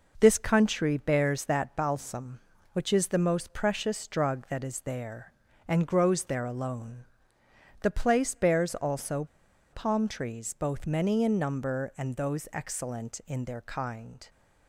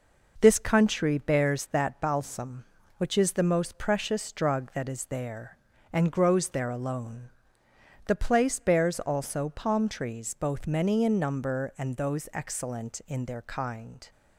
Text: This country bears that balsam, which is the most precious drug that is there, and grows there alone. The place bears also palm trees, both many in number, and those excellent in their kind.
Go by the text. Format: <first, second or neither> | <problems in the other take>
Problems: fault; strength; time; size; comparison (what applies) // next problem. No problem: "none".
second | pauses between "also" and "palm"; noticeable; at 9.2 s; 0.46 s long